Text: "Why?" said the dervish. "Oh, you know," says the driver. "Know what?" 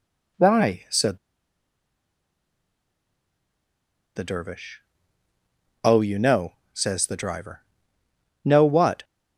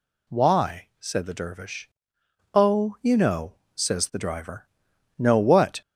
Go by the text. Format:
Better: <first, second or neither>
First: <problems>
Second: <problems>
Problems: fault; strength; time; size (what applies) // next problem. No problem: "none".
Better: second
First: pauses between "said" and "the"; strong; at 1.1 s; 2.9 s long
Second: none